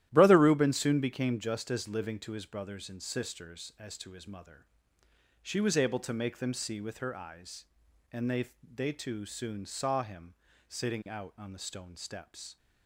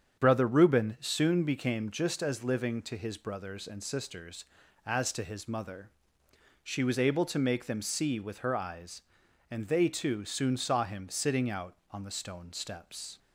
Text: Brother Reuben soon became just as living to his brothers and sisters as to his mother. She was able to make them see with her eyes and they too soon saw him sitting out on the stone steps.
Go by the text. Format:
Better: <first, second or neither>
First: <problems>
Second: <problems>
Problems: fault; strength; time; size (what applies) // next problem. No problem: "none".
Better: second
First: starts louder than the rest; strong; until 1.1 s; 13 dB // says "they" twice; at 8.6 s // pauses between "him" and "sitting"; slight; at 10.3 s; 0.34 s long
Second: starts louder than the rest; strong; until 1.2 s; 7.5 dB